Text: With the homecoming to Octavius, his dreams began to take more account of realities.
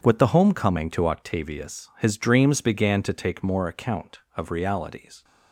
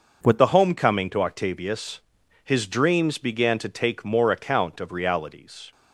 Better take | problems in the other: first | changes voice at "the"; from 0.3 s on; 5.4 s long

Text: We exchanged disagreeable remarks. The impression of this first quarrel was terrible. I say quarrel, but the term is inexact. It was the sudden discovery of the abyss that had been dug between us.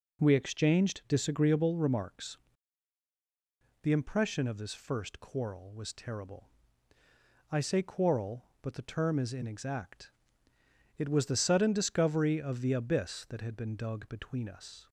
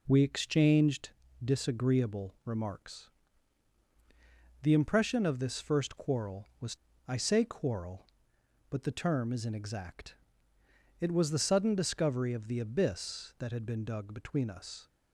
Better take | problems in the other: first | pauses between "exchanged" and "disagreeable"; slight; at 1.0 s; 0.36 s long // skips "terrible"; at 6.9 s

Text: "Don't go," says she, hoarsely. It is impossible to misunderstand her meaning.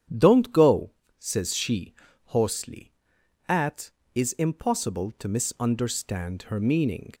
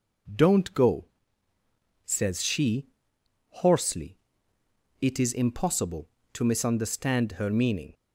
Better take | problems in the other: second | starts louder than the rest; strong; until 1.4 s; 9 dB // says "At" for "It"; at 3.4 s

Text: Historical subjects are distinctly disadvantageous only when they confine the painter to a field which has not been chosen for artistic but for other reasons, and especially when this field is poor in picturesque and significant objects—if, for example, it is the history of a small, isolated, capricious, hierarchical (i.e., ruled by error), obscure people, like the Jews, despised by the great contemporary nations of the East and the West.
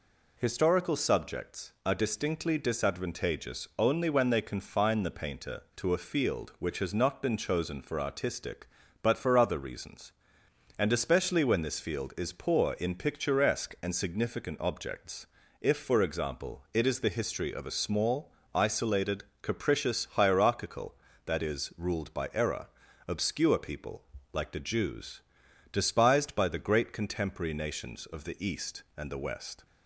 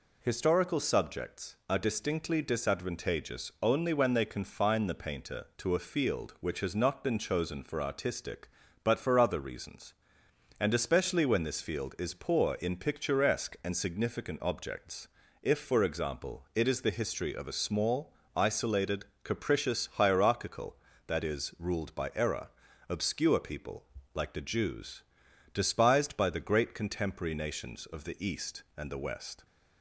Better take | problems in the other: neither | none

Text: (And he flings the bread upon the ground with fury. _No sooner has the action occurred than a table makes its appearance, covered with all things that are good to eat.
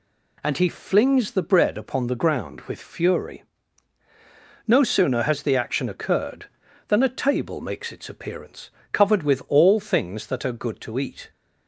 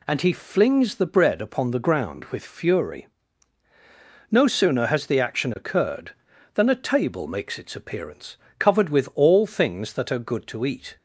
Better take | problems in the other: neither | none

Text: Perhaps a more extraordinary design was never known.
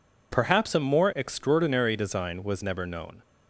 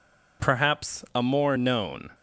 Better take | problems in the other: first | skips "extraordinary design was never"; at 1.5 s

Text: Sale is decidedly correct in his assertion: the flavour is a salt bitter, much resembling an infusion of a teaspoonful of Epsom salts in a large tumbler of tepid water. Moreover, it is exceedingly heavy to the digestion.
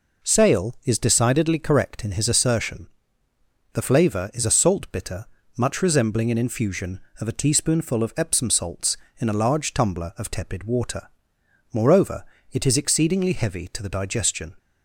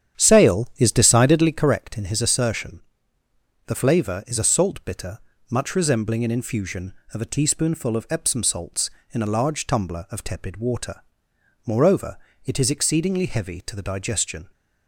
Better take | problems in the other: first | starts louder than the rest; strong; until 1.7 s; 9 dB

